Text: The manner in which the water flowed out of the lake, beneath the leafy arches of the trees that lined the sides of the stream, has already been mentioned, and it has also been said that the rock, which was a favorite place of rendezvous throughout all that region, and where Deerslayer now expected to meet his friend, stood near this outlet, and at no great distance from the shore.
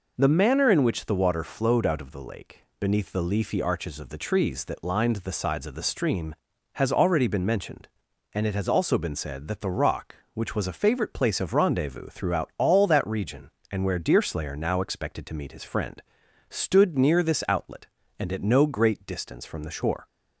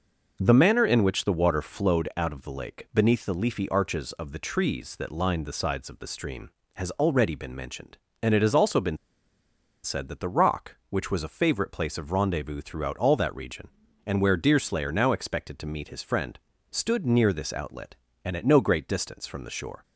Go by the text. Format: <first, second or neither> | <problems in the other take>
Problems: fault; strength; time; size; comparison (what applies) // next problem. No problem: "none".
first | pauses between "been" and "said"; noticeable; at 8.9 s; 0.87 s long